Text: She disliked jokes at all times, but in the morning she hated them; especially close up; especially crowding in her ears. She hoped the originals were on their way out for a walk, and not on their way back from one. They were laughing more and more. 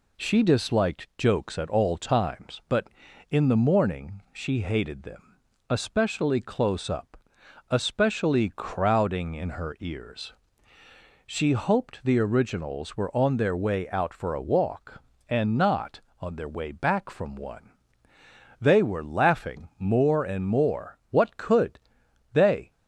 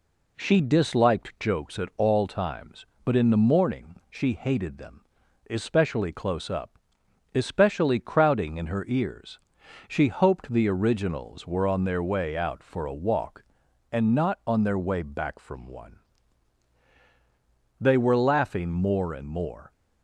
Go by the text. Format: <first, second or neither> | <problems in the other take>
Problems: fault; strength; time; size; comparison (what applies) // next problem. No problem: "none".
second | goes on to say "What could they"; from 21.0 s on; 1.6 s long